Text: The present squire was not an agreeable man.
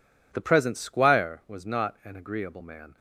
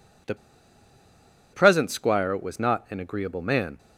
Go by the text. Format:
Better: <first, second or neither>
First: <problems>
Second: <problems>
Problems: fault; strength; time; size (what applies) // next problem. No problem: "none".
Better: first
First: none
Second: pauses between "The" and "present"; at 0.3 s; 1.1 s long